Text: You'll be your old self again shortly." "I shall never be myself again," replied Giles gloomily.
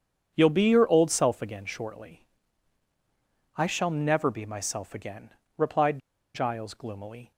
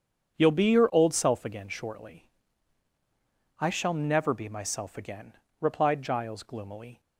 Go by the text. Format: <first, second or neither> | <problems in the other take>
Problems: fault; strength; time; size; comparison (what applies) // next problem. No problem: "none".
second | starts louder than the rest; strong; until 1.3 s; 7.5 dB; strong in the second // pauses between "replied" and "Giles"; slight; at 5.9 s; 0.35 s long